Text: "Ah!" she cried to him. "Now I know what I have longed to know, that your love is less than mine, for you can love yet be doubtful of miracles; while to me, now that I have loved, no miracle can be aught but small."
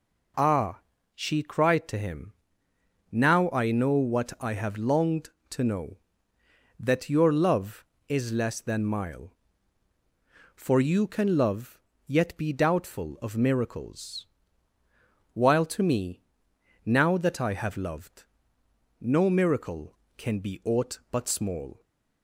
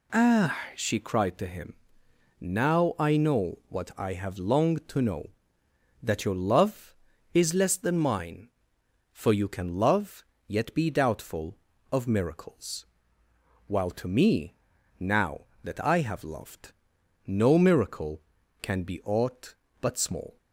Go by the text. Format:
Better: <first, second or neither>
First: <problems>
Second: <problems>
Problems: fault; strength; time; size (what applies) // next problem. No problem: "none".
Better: second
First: says "mile" for "mine"; at 8.8 s // pauses between "love" and "yet"; slight; at 11.7 s; 0.26 s long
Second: pauses between "love" and "yet"; slight; at 10.2 s; 0.24 s long